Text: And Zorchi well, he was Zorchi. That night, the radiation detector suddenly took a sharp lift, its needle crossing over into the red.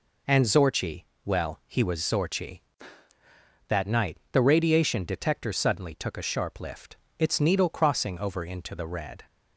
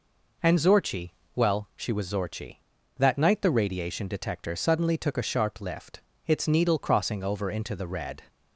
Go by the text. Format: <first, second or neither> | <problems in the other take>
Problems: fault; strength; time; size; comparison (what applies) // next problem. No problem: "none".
first | pauses between "Zorchi" and "well"; slight; at 1.1 s; 0.22 s long; slight in the first // says "she" for "he"; at 1.7 s